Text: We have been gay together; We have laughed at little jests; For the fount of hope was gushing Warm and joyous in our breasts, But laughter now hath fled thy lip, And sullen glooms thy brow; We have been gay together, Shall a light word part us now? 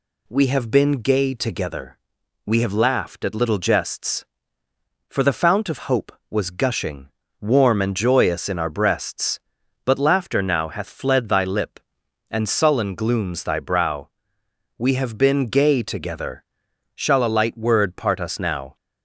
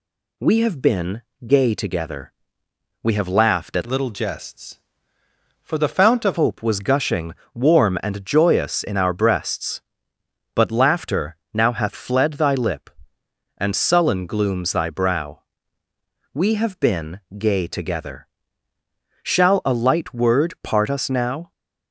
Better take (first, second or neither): first